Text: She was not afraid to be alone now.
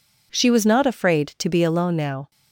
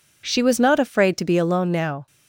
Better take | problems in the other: neither | none

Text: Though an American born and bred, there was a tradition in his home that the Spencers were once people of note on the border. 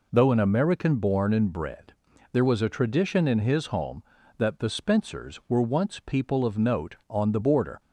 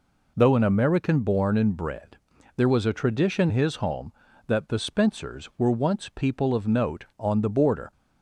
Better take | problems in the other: first | skips "in"; at 3.4 s

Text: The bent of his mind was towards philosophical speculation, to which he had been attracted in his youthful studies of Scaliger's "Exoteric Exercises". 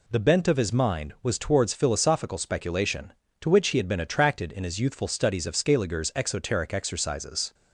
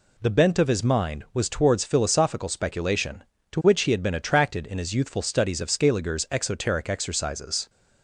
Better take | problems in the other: neither | none

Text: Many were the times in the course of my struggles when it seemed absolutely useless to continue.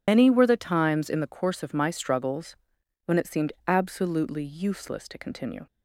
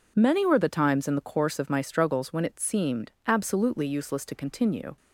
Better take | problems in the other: second | loses the start of "Many"; at 0.0 s; 135 ms // pauses between "struggles" and "when"; noticeable; at 2.5 s; 0.48 s long // pauses between "seemed" and "absolutely"; slight; at 3.5 s; 0.15 s long

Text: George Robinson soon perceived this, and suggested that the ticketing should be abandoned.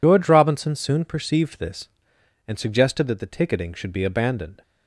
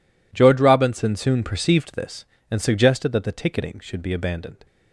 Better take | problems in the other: second | loses the start of "George"; at 0.0 s; 75 ms

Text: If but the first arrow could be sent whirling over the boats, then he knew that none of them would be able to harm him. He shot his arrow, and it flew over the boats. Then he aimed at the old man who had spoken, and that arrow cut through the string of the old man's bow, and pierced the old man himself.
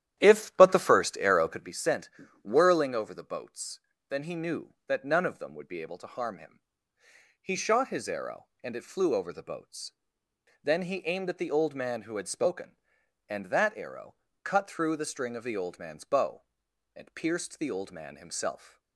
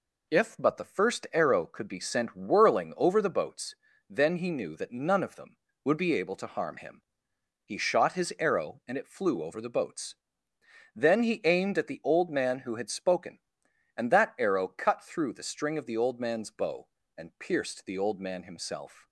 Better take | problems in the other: second | starts louder than the rest; strong; until 1.7 s; 11 dB // pauses between "sent" and "whirling"; slight; at 2.0 s; 0.32 s long // pauses between "arrow" and "cut"; slight; at 14.1 s; 0.28 s long

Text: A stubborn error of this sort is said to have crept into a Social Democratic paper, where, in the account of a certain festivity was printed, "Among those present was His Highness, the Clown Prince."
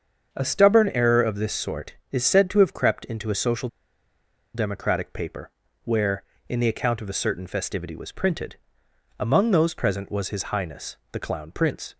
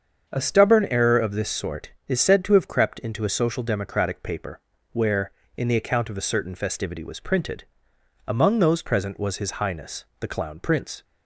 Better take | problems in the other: second | starts louder than the rest; until 1.3 s; 7 dB; also in the second // pauses between "Social" and "Democratic"; noticeable; at 3.6 s; 0.87 s long

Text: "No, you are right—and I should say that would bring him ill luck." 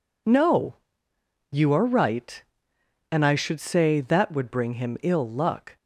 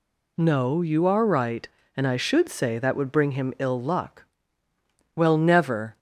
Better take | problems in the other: first | goes on to say "Well never"; noticeable; from 5.1 s on; 0.84 s long

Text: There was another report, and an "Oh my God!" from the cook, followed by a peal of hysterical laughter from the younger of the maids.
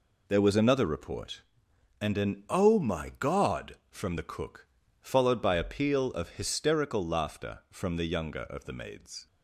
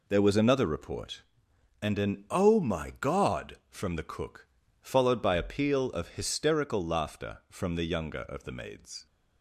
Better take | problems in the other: neither | none

